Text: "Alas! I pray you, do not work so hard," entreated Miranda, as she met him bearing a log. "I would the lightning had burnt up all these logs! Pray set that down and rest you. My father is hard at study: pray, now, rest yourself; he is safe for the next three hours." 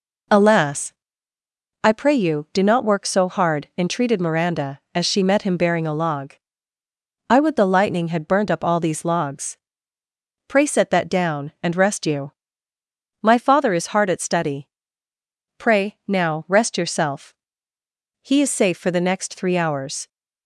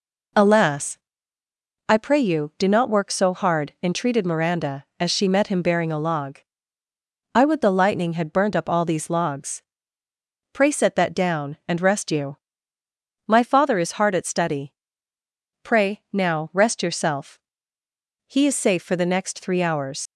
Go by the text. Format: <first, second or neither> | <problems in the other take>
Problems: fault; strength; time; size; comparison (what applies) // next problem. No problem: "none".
first | leaves "hours" unfinished; at 20.0 s; 75 ms